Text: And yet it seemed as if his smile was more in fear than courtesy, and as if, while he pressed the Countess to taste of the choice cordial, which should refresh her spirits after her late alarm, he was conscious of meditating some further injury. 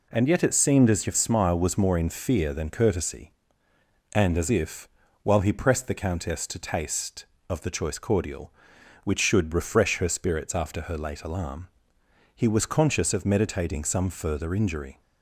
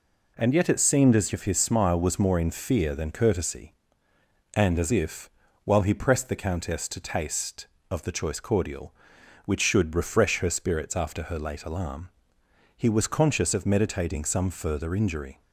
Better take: second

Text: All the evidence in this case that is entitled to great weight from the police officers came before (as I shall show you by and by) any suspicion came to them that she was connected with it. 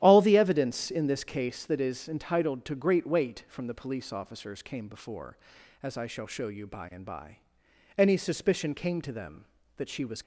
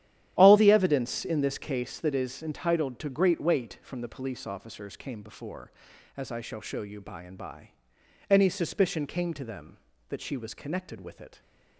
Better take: second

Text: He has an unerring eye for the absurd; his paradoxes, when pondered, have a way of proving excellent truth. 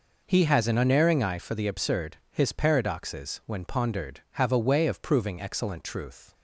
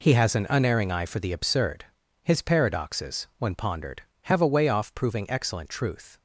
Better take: first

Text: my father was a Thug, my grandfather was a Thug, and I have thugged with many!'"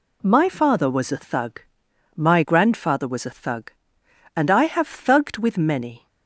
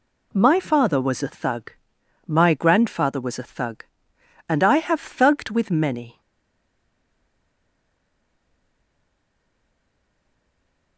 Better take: first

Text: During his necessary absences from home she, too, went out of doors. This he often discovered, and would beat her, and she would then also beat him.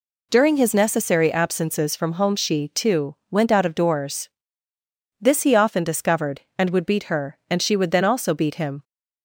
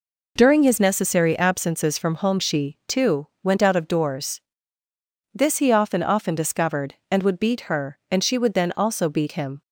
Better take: first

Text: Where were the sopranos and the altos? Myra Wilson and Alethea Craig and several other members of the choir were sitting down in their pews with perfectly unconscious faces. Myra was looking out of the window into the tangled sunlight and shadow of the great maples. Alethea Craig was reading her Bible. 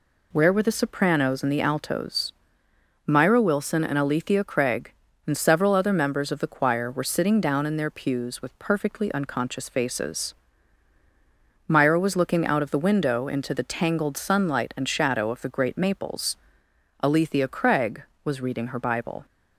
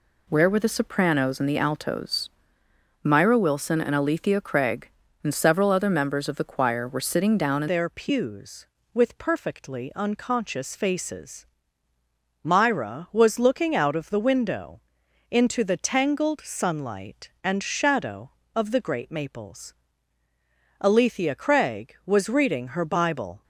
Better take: first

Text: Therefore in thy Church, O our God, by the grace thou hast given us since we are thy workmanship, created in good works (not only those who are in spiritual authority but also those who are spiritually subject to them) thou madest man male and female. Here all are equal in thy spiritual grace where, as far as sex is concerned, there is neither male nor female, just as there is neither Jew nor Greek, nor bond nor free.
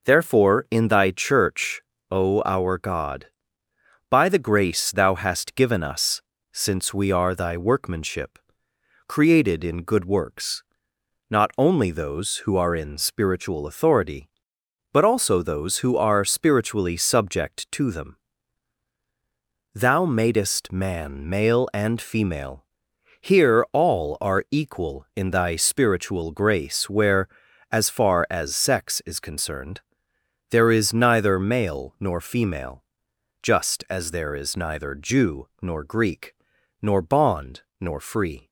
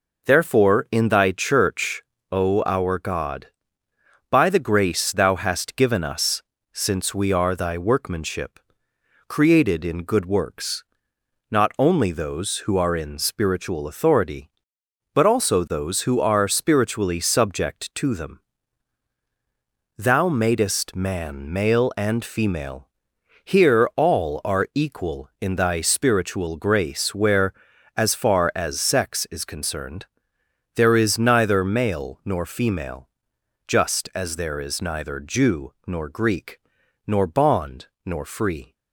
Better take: neither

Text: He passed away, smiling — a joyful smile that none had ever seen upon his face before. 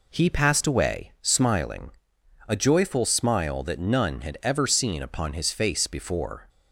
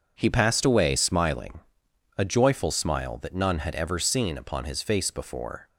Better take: neither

